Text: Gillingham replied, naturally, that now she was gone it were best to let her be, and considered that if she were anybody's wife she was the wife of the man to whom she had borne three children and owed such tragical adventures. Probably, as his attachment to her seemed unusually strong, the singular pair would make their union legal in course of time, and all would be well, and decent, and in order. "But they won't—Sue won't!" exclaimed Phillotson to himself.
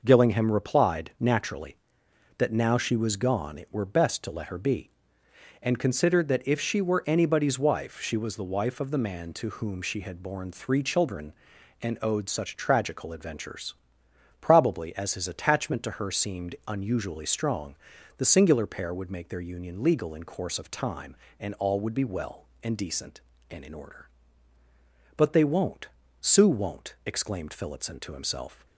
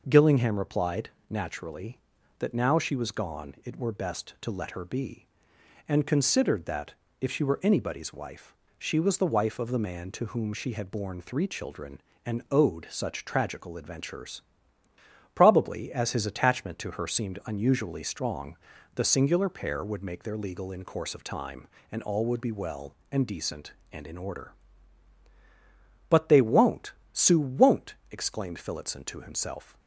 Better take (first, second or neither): first